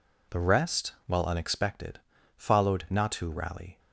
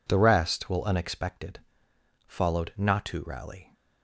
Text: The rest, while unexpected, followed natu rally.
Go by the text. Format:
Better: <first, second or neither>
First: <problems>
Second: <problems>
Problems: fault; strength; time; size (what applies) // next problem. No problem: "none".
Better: first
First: none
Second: says "will" for "while"; at 0.6 s